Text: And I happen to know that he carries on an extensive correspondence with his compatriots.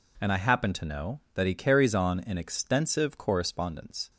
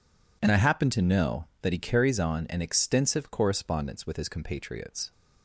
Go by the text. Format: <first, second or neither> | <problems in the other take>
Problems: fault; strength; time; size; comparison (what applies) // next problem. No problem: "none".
second | stops before "with his compatriots"; at 4.1 s